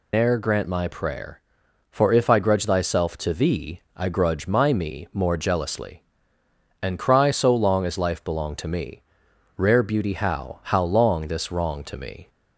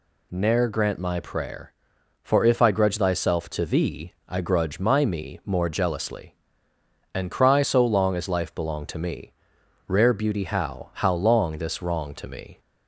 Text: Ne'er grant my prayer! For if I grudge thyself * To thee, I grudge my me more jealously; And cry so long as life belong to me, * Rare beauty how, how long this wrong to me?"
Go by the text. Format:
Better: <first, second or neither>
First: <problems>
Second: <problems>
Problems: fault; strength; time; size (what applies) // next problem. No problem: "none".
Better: second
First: loses the start of "Ne'er"; at 0.1 s; 130 ms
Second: none